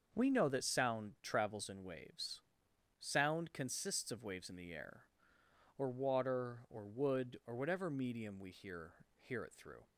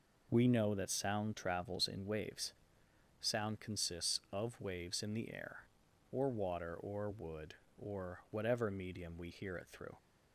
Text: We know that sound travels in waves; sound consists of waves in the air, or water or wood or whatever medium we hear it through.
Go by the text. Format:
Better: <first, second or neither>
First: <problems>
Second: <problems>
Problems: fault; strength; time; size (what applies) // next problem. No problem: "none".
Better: second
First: starts louder than the rest; until 1.1 s; 6.5 dB // says "hear" twice; at 9.1 s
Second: none